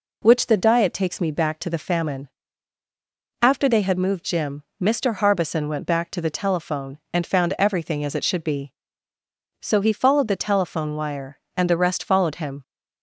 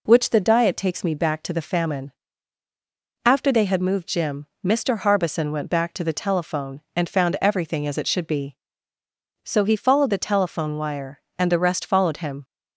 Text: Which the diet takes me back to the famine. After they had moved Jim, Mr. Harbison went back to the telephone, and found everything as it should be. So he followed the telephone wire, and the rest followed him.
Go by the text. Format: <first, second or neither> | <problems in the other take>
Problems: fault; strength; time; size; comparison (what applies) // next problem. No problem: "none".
neither | none